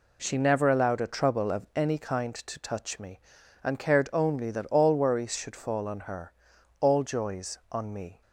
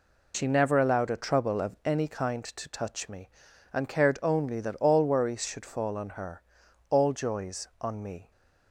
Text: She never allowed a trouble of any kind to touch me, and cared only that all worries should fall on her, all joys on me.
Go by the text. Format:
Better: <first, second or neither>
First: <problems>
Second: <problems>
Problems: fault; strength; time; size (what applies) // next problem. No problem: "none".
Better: first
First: none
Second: loses the start of "She"; at 0.3 s; 55 ms